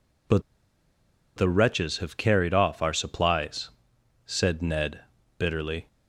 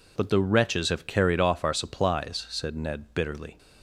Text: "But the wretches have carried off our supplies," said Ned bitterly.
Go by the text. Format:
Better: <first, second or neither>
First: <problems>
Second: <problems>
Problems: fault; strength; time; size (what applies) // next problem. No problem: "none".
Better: second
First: pauses between "But" and "the"; noticeable; at 0.4 s; 0.96 s long // pauses between "Ned" and "bitterly"; at 4.9 s; 0.40 s long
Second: none